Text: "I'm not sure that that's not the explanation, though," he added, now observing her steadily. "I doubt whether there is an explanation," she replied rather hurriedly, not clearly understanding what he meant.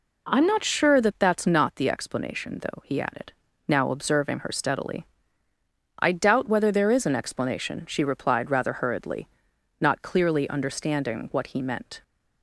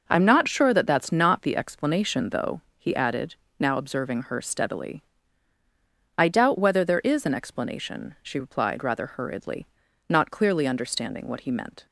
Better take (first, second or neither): neither